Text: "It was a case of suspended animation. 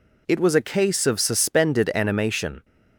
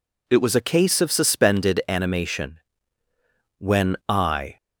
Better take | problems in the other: first | goes on to say "When I"; noticeable; from 3.5 s on; 0.98 s long

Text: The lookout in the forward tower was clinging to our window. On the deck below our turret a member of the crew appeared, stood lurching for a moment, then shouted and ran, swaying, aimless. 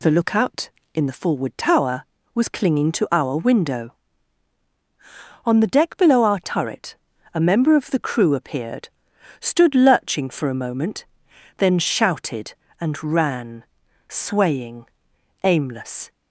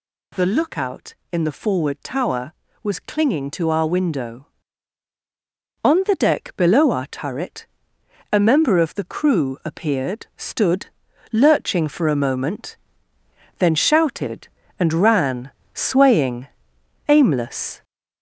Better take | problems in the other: first | gets louder; noticeable; throughout; 4.5 dB // pauses between "turret" and "a"; noticeable; at 7.6 s; 0.64 s long; also in the first // pauses between "stood" and "lurching"; at 10.8 s; 0.44 s long

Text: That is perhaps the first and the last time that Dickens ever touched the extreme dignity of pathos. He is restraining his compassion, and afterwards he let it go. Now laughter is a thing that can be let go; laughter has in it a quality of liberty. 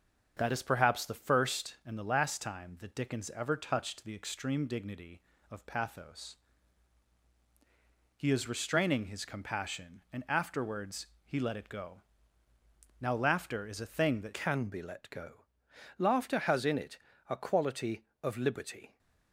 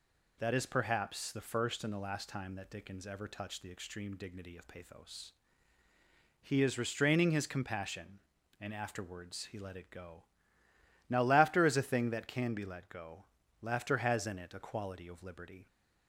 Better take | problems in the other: second | starts louder than the rest; until 1.3 s; 7 dB // pauses between "afterwards" and "he"; slight; at 11.0 s; 0.18 s long // changes voice at "can"; from 14.3 s on; 4.6 s long // pauses between "it" and "a"; slight; at 16.9 s; 0.32 s long

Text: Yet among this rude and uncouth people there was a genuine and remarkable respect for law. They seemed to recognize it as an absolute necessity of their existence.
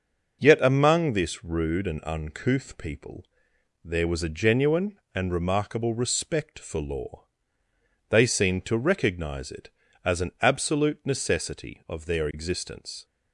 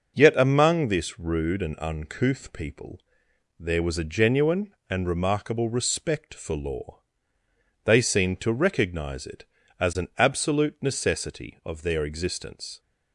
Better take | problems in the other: neither | pauses between "people" and "there"; noticeable; the same in both

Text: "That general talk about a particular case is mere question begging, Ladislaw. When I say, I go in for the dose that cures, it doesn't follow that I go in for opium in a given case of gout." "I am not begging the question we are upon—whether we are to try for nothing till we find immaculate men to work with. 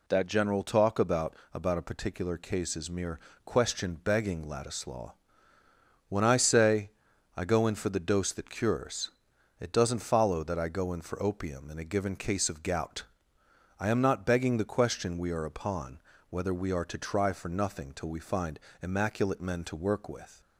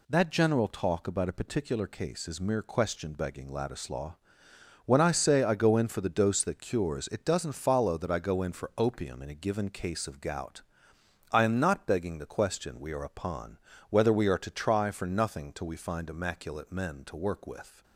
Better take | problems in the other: second | says "about" twice; at 1.5 s // pauses between "mere" and "question"; slight; at 3.1 s; 0.26 s long // pauses between "find" and "immaculate"; slight; at 18.6 s; 0.22 s long

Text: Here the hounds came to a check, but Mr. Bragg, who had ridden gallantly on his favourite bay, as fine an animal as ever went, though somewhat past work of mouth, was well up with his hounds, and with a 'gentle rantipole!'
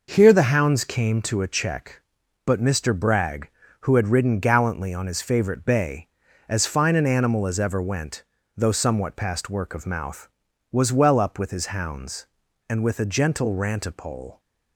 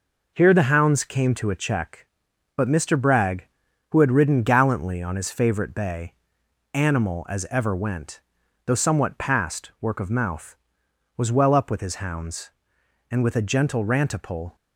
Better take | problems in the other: first | skips "as fine an"; at 6.4 s

